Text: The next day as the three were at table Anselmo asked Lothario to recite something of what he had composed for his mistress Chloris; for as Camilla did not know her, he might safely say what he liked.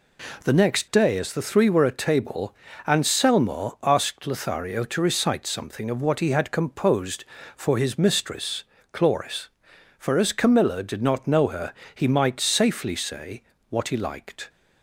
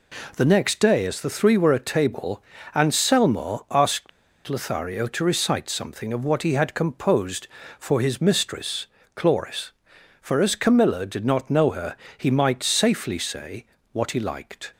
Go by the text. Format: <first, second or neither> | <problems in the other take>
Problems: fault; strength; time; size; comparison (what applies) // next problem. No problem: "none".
first | pauses between "table" and "Anselmo"; slight; at 2.4 s; 0.32 s long; slight in the first // pauses between "asked" and "Lothario"; at 4.0 s; 0.37 s long // pauses between "mistress" and "Chloris"; slight; at 8.8 s; 0.28 s long; slight in the first // pauses between "say" and "what"; slight; at 13.6 s; 0.26 s long; slight in the first